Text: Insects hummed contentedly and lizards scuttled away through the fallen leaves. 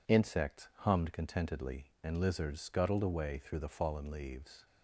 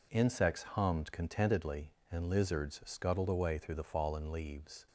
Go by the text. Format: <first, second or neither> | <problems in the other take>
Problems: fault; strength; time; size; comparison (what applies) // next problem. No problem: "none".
neither | none